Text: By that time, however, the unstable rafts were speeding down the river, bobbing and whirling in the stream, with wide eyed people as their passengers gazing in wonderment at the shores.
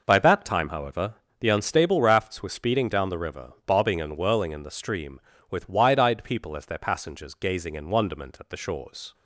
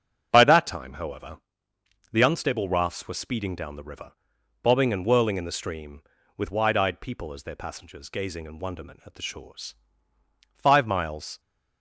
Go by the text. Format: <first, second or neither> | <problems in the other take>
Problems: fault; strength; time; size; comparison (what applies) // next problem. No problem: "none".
first | starts louder than the rest; until 1.3 s; 7 dB // goes on to say "Five miles"; noticeable; from 10.5 s on; 0.84 s long